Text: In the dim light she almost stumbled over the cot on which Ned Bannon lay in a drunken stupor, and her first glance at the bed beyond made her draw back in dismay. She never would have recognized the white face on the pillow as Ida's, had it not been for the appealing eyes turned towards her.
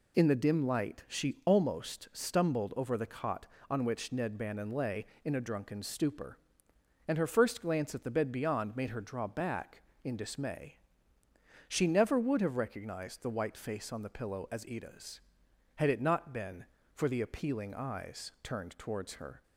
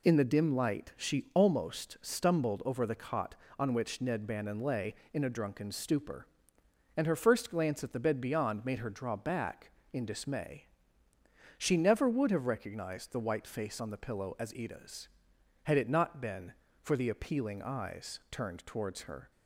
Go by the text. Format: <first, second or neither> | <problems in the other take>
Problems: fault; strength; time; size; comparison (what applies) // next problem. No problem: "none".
neither | none